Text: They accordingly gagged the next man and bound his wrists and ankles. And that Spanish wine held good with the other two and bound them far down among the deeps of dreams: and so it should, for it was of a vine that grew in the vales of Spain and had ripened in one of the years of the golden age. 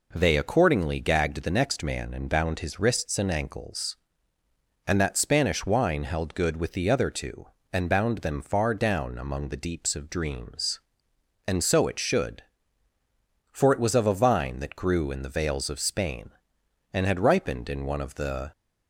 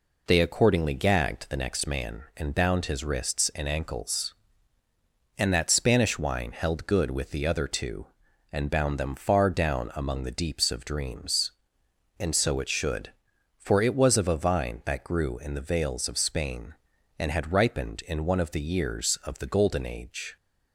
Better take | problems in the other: second | stops before "years of the golden age"; at 18.5 s

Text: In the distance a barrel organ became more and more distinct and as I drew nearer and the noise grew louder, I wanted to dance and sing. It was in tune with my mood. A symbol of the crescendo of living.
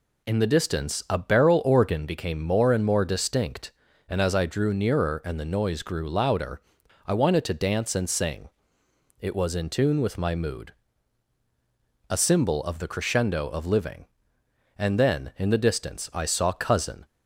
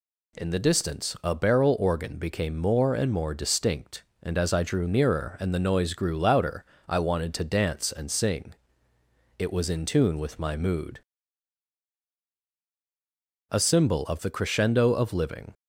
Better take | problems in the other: second | goes on to say "And then in the distance I saw Cousin"; strong; from 14.7 s on; 2.2 s long

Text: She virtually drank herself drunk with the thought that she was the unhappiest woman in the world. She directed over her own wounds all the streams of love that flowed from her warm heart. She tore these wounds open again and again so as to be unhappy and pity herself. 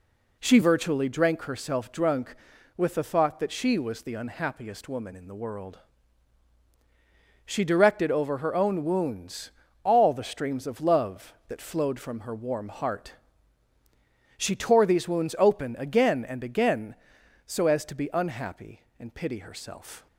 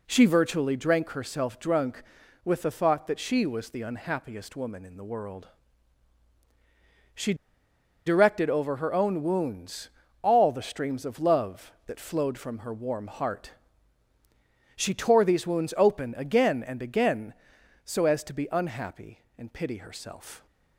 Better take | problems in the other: first | pauses between "She" and "directed"; noticeable; at 7.3 s; 0.72 s long // pauses between "wounds" and "all"; slight; at 9.8 s; 0.32 s long; slight in the first

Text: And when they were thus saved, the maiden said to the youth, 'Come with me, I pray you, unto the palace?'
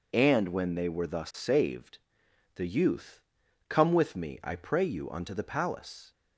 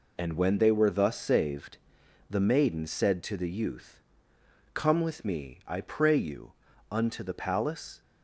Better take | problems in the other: second | skips "the maiden said to"; at 2.2 s

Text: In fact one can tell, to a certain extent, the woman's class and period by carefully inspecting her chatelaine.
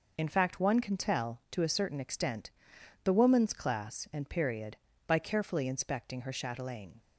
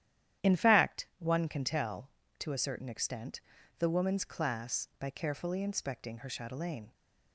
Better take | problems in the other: first | starts louder than the rest; strong; until 1.5 s; 11 dB // skips "and period"; at 4.9 s

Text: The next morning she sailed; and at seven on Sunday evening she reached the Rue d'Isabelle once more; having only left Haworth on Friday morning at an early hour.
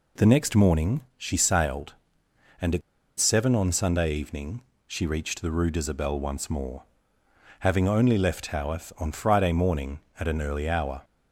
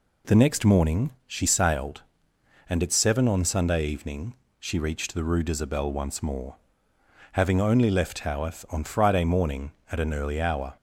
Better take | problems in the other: second | pauses between "morning" and "she"; slight; at 1.0 s; 0.16 s long; slight in the second // pauses between "at" and "seven"; at 2.8 s; 0.38 s long // pauses between "evening" and "she"; slight; at 4.5 s; 0.26 s long; slight in the second

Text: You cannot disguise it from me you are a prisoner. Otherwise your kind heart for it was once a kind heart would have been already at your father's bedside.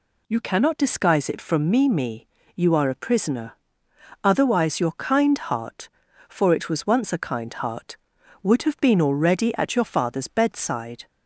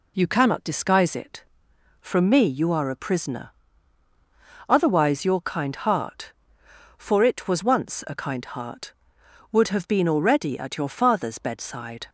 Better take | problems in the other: second | says "me" twice; at 1.8 s

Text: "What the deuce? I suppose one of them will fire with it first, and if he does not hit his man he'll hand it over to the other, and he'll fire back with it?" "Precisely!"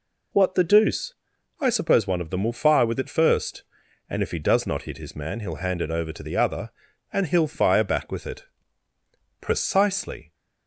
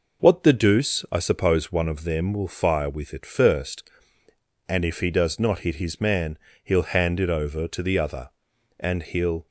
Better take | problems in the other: first | pauses between "man" and "he'll"; slight; at 6.3 s; 0.26 s long // stops before "fire back with it Precisely"; at 9.4 s

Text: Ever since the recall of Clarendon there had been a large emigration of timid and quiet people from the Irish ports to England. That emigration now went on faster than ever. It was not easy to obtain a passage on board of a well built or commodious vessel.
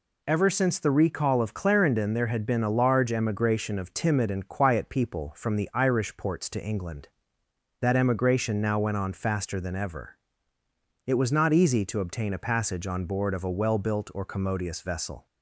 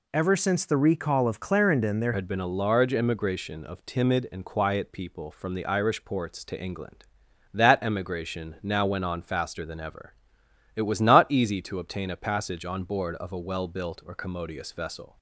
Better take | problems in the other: first | changes voice at "had"; from 2.1 s on; 13.0 s long

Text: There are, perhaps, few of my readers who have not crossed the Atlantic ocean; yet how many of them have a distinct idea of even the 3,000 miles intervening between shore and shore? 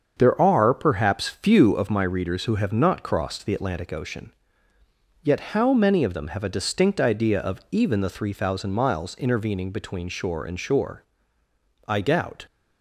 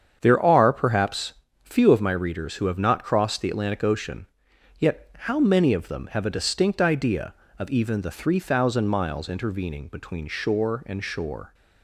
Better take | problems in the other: second | starts louder than the rest; until 1.2 s; 7 dB; strong in the second // goes on to say "I doubt"; from 11.8 s on; 0.60 s long

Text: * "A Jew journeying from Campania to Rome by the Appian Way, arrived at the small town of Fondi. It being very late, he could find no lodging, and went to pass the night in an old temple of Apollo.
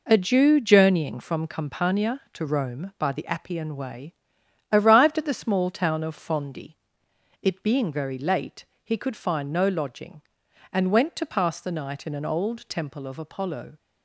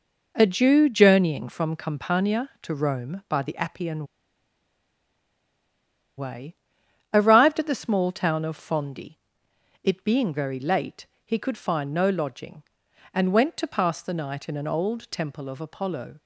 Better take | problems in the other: first | pauses between "Appian" and "Way"; strong; at 4.0 s; 2.1 s long

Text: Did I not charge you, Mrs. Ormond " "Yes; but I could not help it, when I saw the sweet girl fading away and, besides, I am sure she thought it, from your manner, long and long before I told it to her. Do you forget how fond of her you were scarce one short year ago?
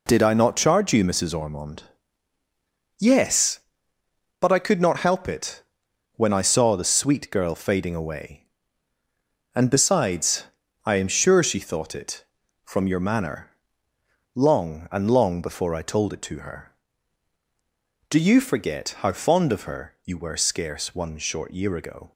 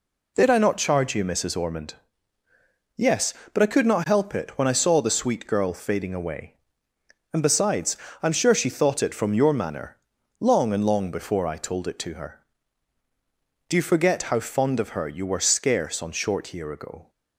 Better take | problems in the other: first | says "on" for "one"; at 16.0 s

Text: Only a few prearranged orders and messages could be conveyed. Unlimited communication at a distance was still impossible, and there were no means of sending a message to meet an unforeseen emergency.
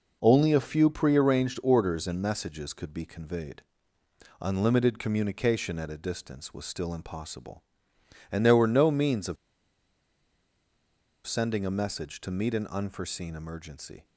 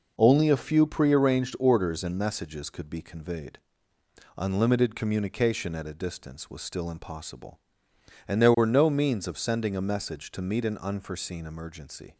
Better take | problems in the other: second | pauses between "of" and "sending"; strong; at 9.3 s; 1.9 s long

